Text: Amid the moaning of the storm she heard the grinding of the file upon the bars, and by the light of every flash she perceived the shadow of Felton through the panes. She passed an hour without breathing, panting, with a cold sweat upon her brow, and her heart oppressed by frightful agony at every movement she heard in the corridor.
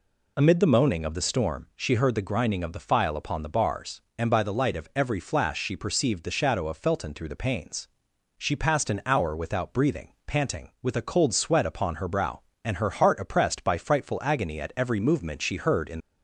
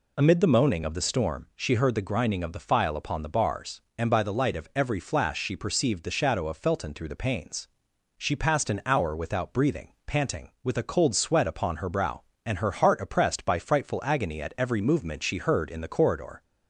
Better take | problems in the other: second | stops before "the corridor"; at 15.9 s

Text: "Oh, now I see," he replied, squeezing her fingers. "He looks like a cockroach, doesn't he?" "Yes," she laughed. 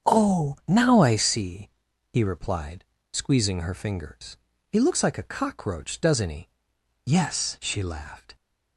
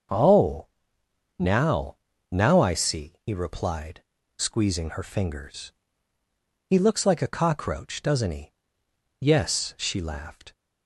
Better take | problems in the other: first | starts louder than the rest; until 1.8 s; 6.5 dB; strong in the first // says "now" twice; at 2.3 s

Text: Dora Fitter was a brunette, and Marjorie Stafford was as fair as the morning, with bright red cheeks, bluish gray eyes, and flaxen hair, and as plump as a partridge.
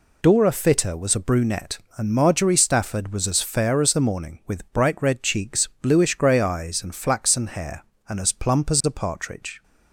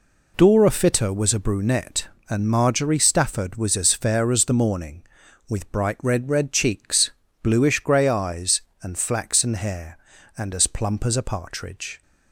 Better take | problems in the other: first | says "red" twice; at 6.2 s

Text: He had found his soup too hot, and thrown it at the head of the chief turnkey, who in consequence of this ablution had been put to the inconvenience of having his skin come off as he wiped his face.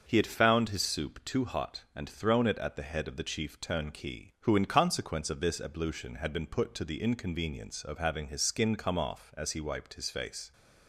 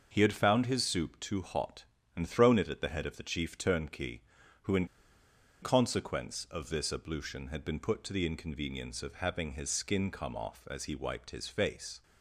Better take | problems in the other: first | starts louder than the rest; until 1.1 s; 6.5 dB; also in the first // pauses between "in" and "consequence"; noticeable; at 4.8 s; 0.76 s long

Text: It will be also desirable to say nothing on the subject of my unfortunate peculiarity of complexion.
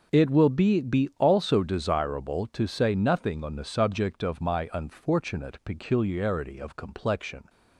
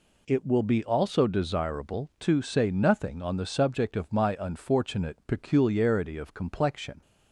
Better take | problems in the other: second | says "be" twice; at 0.8 s

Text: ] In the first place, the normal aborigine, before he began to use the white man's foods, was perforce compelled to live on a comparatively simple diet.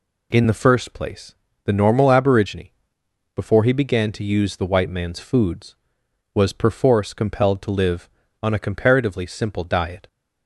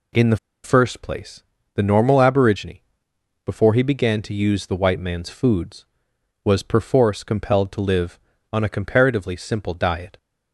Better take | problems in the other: first | pauses between "the" and "first"; slight; at 0.3 s; 0.27 s long

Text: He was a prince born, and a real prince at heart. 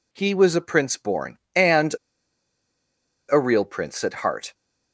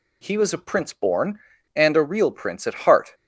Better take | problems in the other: second | pauses between "and" and "a"; strong; at 1.9 s; 1.3 s long

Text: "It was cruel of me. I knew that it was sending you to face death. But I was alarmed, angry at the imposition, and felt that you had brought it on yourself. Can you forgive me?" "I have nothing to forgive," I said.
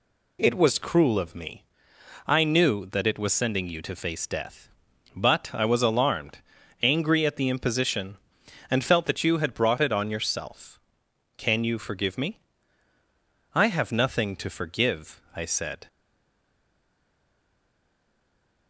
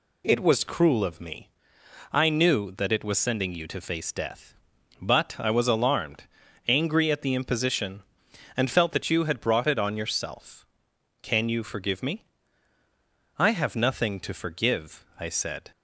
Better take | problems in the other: second | stays silent after the last word; strong; from 15.8 s on; 2.8 s long

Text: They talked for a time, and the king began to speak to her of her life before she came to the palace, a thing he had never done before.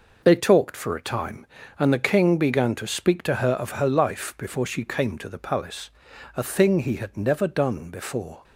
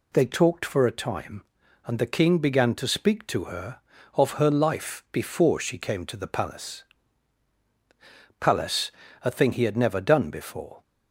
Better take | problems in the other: first | says "palace" twice; at 8.3 s

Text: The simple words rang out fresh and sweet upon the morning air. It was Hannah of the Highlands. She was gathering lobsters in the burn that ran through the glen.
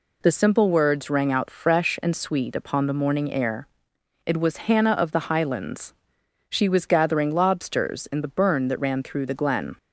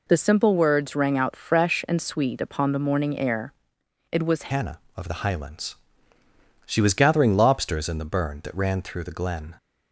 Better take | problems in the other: first | changes voice at "Hannah"; from 4.5 s on; 5.0 s long

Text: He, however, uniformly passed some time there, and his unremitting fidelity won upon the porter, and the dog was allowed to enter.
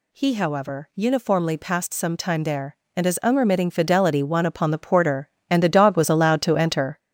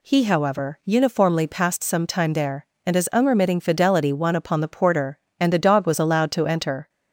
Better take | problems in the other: second | gets louder; throughout; 6.5 dB

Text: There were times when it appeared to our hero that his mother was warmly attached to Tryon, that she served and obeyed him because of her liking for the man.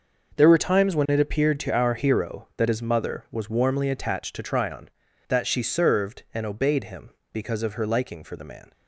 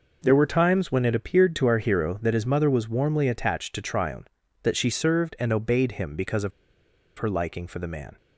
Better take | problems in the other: first | pauses between "of" and "her"; noticeable; at 6.5 s; 0.67 s long

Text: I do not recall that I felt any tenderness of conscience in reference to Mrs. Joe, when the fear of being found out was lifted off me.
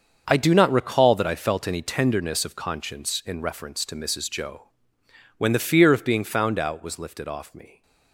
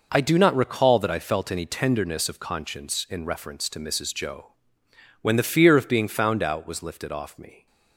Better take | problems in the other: second | gets quieter; strong; throughout; 11 dB

